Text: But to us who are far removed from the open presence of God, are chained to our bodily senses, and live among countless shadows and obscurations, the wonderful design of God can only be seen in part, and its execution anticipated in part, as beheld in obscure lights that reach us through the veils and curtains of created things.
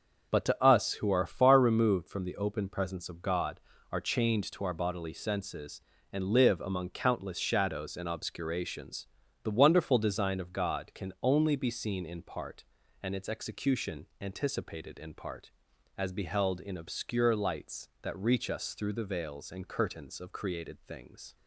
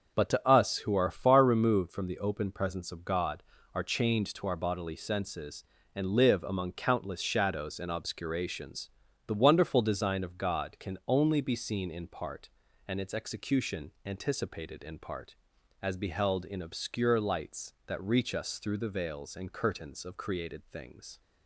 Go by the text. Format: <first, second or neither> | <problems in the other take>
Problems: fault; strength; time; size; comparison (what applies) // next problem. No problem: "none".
neither | starts louder than the rest; the same in both